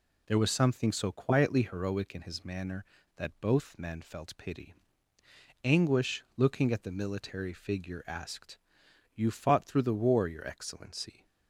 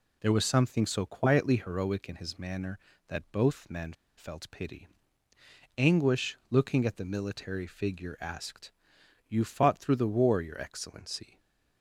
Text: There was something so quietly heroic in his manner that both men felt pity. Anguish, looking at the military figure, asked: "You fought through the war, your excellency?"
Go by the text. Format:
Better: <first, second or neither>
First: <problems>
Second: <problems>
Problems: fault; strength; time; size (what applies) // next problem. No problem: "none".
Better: first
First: none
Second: pauses between "men" and "felt"; slight; at 3.9 s; 0.24 s long